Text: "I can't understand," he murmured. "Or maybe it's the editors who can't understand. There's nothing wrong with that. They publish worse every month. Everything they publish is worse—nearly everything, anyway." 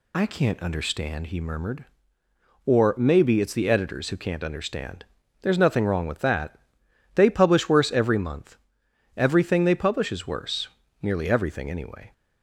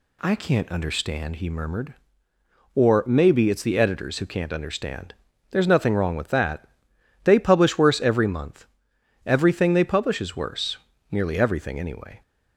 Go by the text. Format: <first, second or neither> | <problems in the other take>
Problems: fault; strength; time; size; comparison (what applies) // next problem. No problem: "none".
second | loses the start of "I"; at 0.1 s; 35 ms